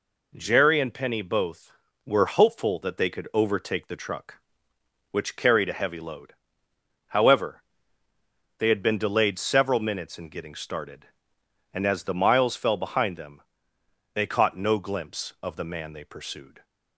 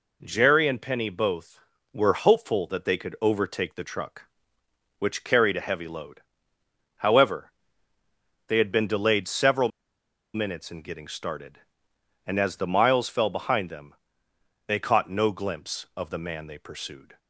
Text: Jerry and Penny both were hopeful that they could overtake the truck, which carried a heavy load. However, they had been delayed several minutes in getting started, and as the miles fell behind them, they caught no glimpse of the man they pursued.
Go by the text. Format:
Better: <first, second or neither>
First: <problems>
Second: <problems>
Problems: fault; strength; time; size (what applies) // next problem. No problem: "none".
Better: first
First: none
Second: pauses between "several" and "minutes"; noticeable; at 9.6 s; 0.66 s long